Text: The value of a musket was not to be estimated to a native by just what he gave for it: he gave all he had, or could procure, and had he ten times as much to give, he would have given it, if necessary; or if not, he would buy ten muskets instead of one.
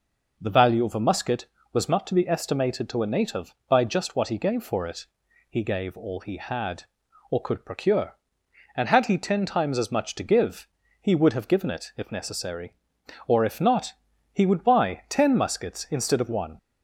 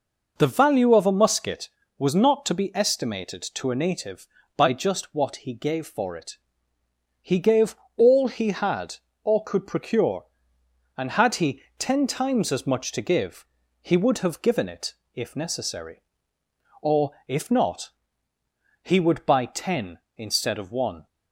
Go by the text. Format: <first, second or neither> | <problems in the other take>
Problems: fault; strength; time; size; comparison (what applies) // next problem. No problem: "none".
first | pauses between "gave" and "all"; slight; at 7.7 s; 0.22 s long // pauses between "he" and "ten"; slight; at 11.6 s; 0.16 s long // pauses between "or" and "if"; slight; at 17.1 s; 0.16 s long // skips "muskets"; at 20.0 s